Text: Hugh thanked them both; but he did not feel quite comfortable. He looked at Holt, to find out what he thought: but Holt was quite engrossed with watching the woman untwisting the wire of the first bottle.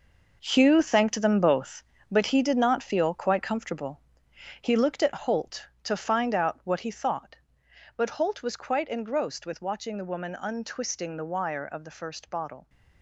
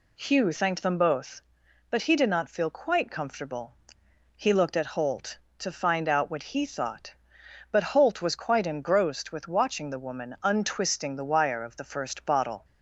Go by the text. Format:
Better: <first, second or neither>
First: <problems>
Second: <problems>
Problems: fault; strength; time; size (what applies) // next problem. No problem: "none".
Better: second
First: gets quieter; strong; throughout; 10.5 dB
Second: none